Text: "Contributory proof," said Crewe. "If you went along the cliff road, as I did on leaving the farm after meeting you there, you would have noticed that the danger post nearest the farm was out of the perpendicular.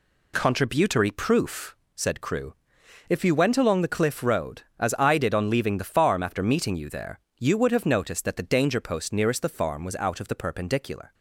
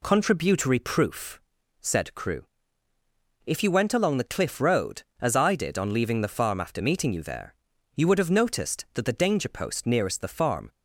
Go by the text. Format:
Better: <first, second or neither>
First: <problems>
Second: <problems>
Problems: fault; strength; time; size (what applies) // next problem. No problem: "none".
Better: first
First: none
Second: stops before "was out of the perpendicular"; at 10.7 s